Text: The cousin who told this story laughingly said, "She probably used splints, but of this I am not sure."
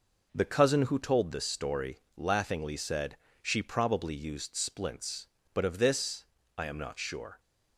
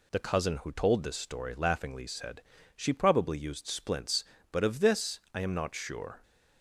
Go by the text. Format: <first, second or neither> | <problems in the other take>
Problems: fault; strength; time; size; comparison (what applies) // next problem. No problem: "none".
second | starts louder than the rest; noticeable; until 1.4 s; 5 dB // pauses between "story" and "laughingly"; slight; at 1.9 s; 0.18 s long // pauses between "this" and "I"; slight; at 6.2 s; 0.32 s long; slight in the second